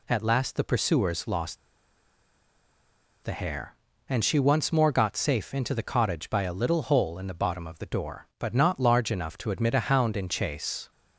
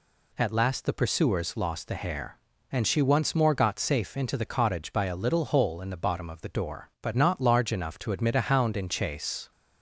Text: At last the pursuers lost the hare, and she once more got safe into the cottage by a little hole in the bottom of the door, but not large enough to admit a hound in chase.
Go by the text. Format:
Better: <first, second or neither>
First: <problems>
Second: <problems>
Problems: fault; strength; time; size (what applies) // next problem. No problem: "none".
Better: second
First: pauses between "lost" and "the"; strong; at 1.5 s; 1.6 s long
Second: none